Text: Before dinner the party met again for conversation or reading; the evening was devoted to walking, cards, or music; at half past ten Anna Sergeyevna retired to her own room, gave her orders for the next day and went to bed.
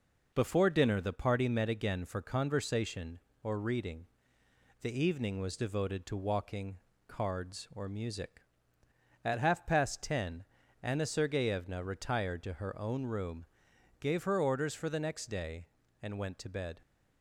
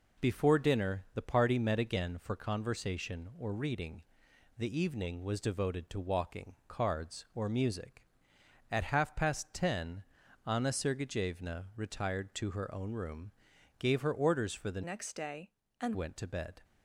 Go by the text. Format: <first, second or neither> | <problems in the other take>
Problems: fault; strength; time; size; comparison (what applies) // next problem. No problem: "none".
first | pauses between "ten" and "Anna"; at 10.0 s; 0.42 s long; slight in the first // changes voice from "next" to "and"; from 14.8 to 15.9 s; 1.1 s long